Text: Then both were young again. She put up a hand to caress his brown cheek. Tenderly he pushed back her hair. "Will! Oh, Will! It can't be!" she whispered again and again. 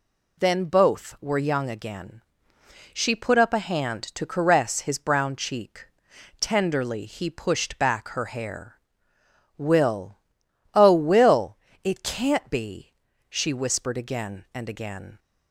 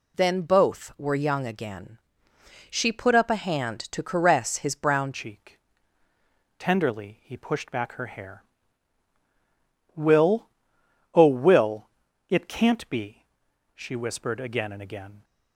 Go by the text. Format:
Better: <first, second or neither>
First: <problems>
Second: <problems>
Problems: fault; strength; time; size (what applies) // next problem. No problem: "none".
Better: first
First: none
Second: changes voice at "cheek"; from 5.1 s on; 10.1 s long